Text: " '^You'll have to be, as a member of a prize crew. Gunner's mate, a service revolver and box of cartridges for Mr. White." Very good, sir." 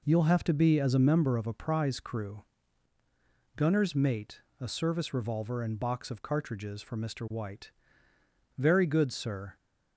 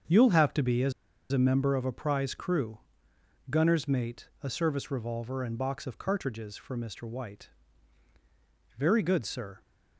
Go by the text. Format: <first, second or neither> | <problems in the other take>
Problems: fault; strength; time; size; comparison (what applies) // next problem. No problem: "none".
first | starts louder than the rest; until 1.4 s; 7 dB // pauses between "as" and "a"; at 0.9 s; 0.38 s long